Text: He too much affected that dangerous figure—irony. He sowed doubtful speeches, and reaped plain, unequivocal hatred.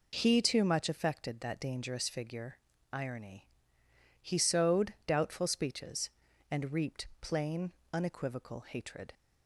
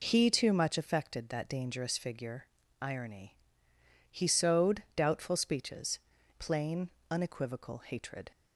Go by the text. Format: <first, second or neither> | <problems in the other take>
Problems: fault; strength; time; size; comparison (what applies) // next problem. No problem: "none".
first | skips "and reaped"; at 6.1 s